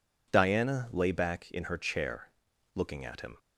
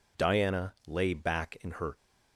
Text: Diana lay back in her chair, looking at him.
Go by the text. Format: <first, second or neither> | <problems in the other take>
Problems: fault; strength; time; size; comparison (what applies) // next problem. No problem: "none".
first | pauses between "Diana" and "lay"; slight; at 0.7 s; 0.16 s long // stops before "chair looking at him"; at 1.9 s